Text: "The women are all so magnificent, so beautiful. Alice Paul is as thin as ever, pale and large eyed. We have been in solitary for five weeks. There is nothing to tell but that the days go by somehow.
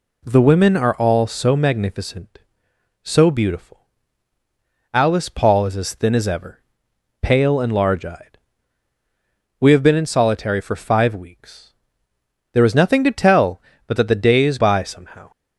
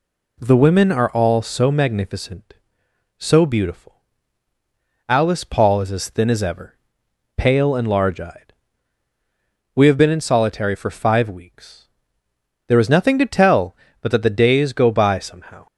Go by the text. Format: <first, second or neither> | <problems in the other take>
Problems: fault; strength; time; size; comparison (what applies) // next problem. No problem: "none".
second | skips "go"; at 14.5 s